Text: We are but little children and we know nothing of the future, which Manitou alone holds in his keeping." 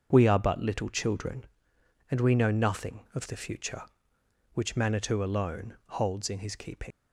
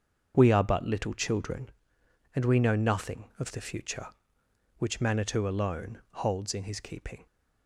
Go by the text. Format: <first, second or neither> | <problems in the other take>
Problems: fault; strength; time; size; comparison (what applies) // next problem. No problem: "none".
second | starts louder than the rest; until 1.1 s; 6.5 dB; also in the second // leaves "keeping" unfinished; at 6.9 s; 105 ms